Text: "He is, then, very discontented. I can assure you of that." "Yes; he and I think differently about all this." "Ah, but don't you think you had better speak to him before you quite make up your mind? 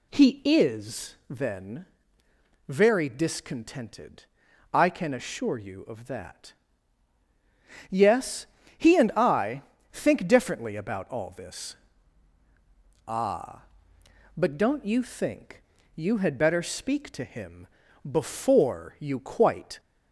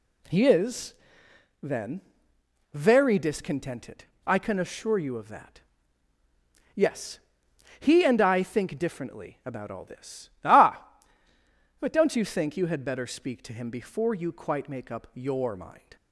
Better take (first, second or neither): second